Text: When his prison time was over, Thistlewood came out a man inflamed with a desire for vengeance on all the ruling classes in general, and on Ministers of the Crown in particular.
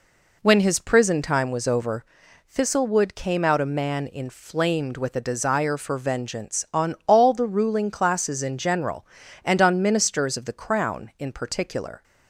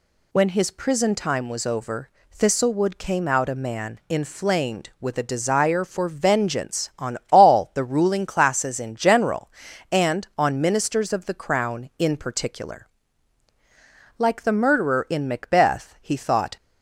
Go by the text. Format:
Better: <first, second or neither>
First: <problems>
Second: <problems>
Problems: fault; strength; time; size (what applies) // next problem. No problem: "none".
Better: first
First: none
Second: goes on to say "Like the murderer in Macbeth he thought"; strong; from 14.1 s on; 2.4 s long